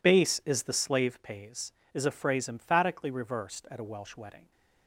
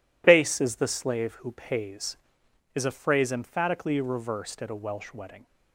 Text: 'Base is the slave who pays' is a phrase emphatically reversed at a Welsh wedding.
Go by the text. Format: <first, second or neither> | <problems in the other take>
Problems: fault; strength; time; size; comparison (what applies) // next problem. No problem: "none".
second | skips "who"; at 1.2 s